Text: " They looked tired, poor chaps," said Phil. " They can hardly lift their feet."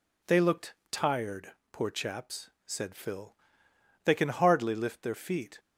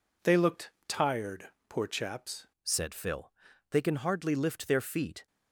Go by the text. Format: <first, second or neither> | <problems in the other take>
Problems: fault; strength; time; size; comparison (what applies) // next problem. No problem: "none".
first | pauses between "looked" and "tired"; slight; at 0.7 s; 0.16 s long; slight in the first // changes voice at "said"; from 2.6 s on; 2.6 s long